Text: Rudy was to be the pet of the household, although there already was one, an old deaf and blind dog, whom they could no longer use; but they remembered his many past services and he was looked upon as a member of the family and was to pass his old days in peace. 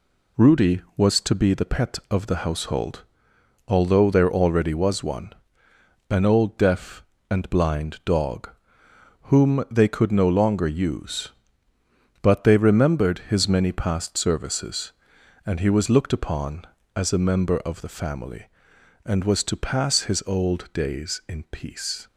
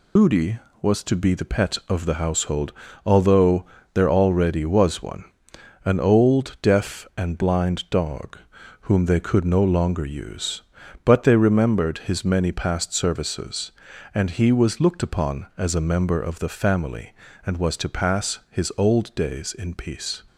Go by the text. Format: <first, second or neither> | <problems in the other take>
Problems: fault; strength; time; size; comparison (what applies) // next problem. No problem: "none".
first | loses the start of "Rudy"; at 0.1 s; 110 ms // pauses between "although" and "there"; slight; at 3.6 s; 0.28 s long